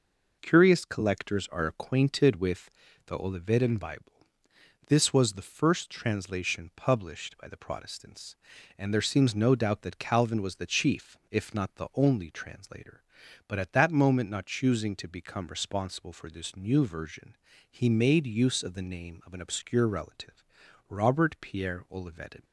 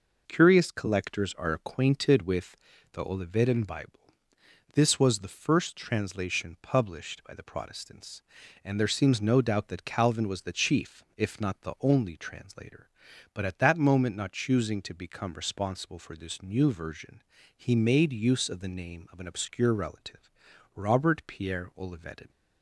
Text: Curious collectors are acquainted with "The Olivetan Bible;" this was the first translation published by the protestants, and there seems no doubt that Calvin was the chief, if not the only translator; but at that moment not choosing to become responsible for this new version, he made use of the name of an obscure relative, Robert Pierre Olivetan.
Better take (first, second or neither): neither